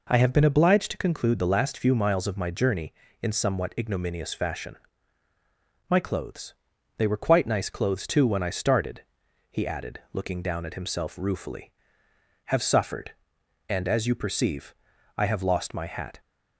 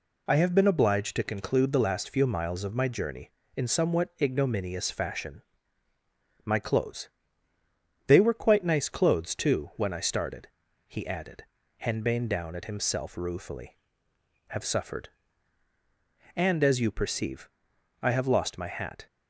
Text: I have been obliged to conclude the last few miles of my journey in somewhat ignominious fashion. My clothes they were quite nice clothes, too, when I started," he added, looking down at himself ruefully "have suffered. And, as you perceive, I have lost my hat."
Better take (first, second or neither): first